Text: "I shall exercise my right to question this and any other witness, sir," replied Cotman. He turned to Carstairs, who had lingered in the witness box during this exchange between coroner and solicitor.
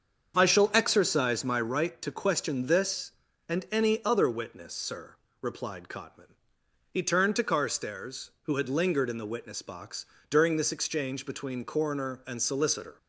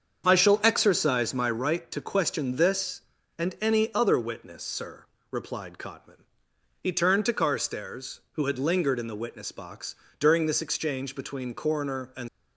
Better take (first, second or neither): first